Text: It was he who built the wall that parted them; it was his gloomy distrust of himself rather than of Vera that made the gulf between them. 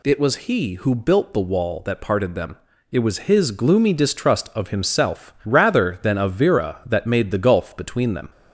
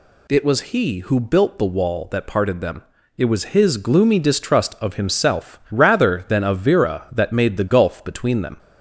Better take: neither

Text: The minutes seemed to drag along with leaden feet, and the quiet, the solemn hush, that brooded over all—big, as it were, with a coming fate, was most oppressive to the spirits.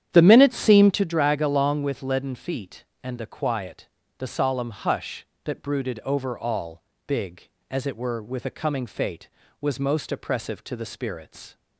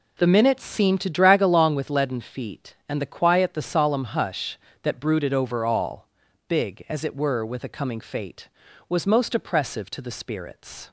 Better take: second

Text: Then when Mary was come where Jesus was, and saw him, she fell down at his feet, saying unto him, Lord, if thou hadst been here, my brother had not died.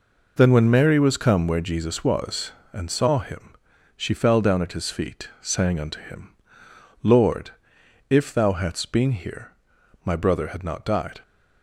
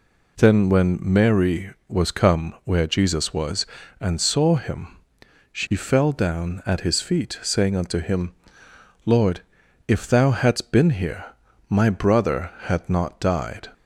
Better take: neither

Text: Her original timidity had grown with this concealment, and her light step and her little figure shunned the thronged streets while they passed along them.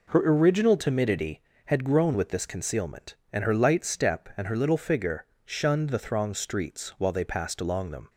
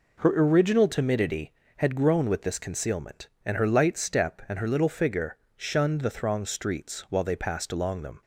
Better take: neither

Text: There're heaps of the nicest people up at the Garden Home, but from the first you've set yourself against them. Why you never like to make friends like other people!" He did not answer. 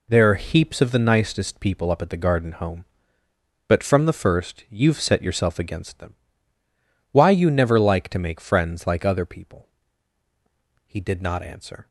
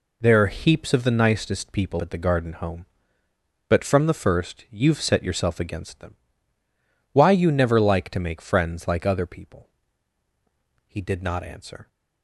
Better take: first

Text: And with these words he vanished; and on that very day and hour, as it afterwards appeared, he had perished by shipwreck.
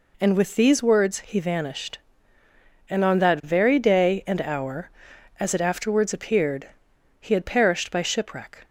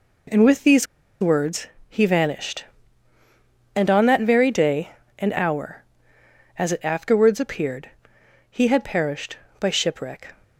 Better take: first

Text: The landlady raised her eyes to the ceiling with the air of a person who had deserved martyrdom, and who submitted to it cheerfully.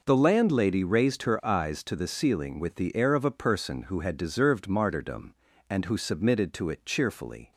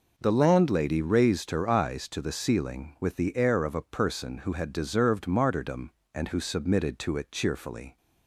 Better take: neither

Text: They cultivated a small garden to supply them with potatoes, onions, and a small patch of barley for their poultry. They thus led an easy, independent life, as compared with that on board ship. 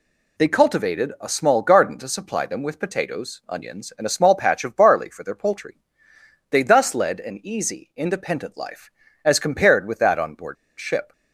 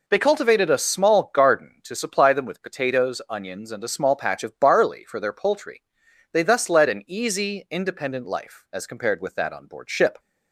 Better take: second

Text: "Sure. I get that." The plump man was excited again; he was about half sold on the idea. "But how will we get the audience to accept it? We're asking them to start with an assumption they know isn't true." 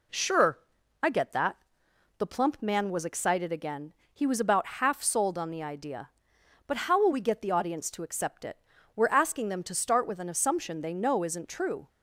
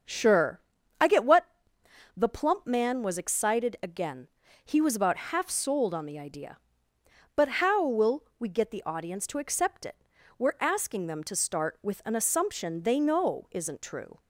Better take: first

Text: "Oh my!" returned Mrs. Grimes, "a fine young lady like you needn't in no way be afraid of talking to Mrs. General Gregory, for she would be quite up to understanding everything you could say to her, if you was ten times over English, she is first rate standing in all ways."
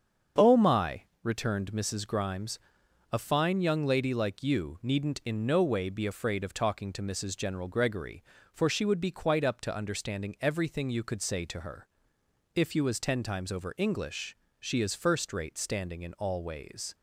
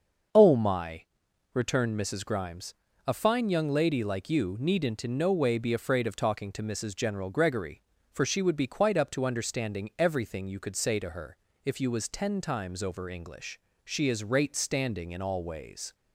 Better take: first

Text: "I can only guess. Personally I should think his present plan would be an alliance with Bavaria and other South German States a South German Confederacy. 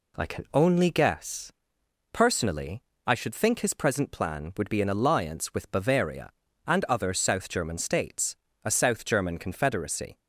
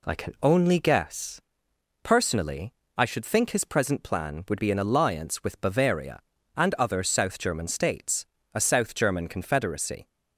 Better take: neither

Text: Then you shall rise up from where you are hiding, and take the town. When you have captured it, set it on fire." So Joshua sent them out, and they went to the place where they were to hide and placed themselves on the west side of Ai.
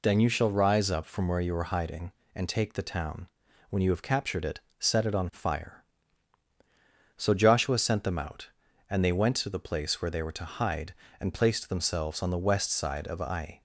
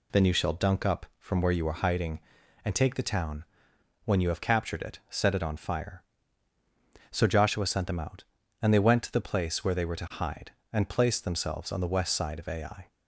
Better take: first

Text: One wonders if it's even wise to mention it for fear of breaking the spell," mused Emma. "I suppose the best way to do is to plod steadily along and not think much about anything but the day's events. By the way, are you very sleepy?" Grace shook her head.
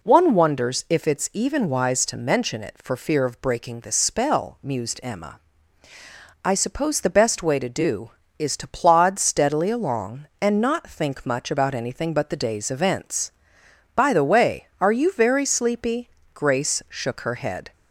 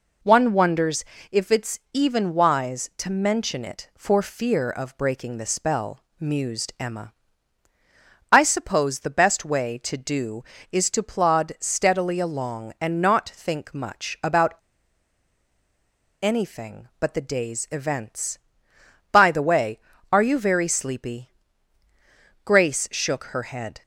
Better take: first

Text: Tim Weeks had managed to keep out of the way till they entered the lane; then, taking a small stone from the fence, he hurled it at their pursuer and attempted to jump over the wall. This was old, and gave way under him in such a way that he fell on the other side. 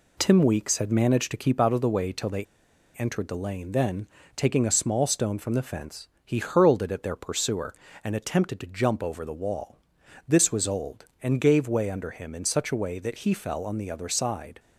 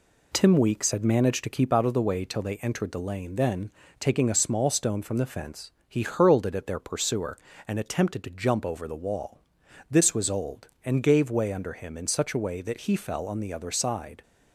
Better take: second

